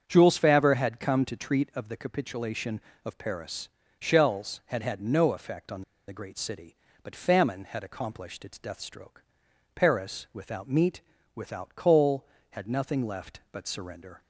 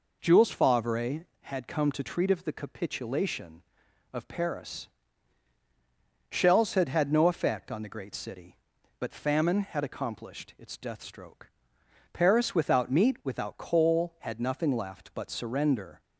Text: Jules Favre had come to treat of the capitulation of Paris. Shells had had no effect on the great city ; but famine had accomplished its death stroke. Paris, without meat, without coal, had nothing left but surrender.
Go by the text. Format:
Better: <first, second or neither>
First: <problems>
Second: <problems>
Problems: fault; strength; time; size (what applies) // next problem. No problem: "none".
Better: second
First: starts louder than the rest; strong; until 1.0 s; 7.5 dB // pauses between "on" and "the"; slight; at 5.8 s; 0.26 s long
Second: none